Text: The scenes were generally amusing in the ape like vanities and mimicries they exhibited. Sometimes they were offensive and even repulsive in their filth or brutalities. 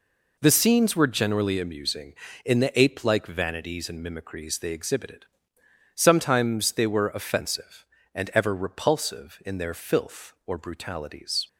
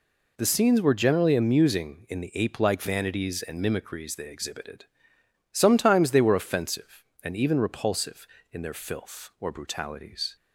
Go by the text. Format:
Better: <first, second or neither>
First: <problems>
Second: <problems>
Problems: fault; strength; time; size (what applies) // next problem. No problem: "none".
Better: second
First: says "ever" for "even"; at 8.3 s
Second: none